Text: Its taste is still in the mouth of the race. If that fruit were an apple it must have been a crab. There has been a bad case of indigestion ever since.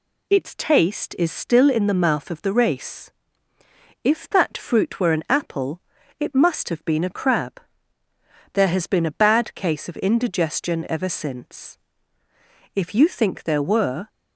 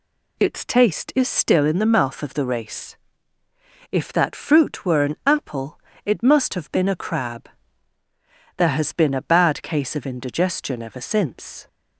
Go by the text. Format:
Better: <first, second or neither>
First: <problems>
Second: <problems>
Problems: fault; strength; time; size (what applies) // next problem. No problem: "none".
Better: second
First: pauses between "apple" and "it"; at 5.7 s; 0.40 s long // goes on to say "If you think there were"; from 12.7 s on; 1.3 s long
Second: pauses between "apple" and "it"; slight; at 5.7 s; 0.26 s long